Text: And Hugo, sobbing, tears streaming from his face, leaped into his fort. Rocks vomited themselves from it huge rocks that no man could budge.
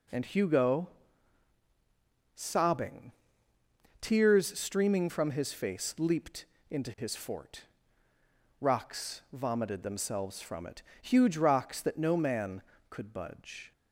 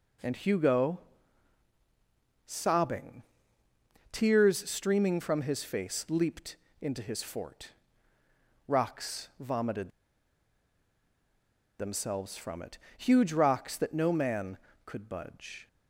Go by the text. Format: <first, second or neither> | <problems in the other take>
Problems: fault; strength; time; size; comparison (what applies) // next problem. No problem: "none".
first | pauses between "leaped" and "into"; slight; at 6.5 s; 0.24 s long; slight in the first // pauses between "vomited" and "themselves"; strong; at 9.9 s; 1.8 s long // pauses between "it" and "huge"; slight; at 12.7 s; 0.20 s long; slight in the first